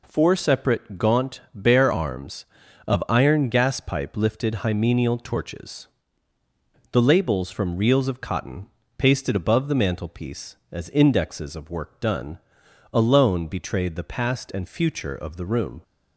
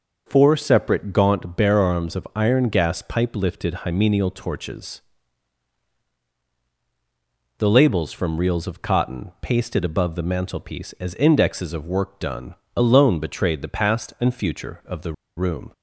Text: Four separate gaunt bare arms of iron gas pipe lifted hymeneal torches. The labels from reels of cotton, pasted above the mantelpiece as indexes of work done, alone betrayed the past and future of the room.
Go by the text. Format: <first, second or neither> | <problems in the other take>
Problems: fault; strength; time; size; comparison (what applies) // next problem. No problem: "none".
first | starts louder than the rest; until 1.2 s; 6 dB // pauses between "the" and "room"; slight; at 15.1 s; 0.24 s long